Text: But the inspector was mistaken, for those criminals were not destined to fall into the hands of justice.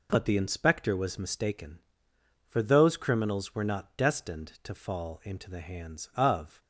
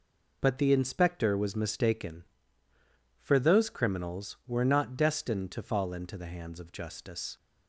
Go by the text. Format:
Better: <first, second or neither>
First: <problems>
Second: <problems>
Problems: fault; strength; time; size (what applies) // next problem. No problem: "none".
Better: second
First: stops before "justice"; at 6.6 s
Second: none